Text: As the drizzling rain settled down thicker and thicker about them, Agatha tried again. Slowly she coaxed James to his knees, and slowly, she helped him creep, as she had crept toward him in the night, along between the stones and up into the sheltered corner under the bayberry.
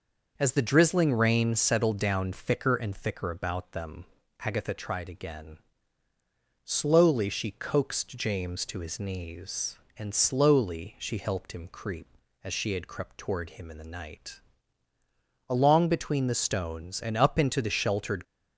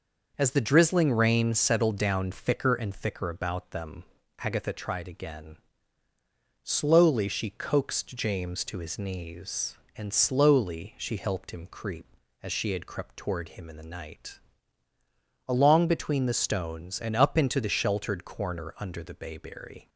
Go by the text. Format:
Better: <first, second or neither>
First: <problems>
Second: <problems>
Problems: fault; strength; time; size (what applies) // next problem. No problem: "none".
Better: second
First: stops before "corner under the bayberry"; at 18.2 s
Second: none